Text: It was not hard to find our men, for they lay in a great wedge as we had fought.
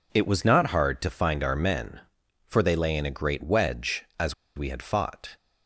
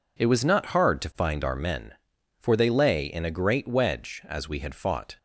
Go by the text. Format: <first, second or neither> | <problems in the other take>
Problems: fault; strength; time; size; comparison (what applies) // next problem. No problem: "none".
second | pauses between "as" and "we"; slight; at 4.3 s; 0.22 s long